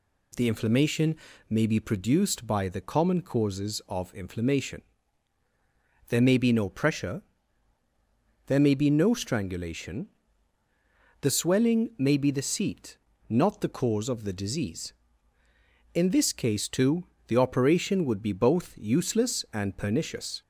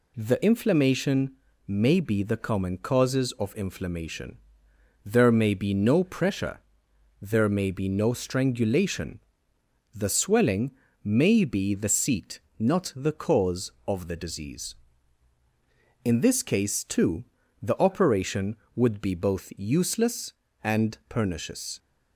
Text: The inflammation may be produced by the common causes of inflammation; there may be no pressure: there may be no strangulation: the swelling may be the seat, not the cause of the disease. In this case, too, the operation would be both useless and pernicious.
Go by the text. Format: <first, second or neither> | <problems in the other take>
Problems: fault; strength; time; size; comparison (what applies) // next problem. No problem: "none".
first | pauses between "inflammation" and "may"; slight; at 1.3 s; 0.36 s long; slight in the first // skips "produced by"; at 2.2 s // pauses between "swelling" and "may"; slight; at 10.7 s; 0.32 s long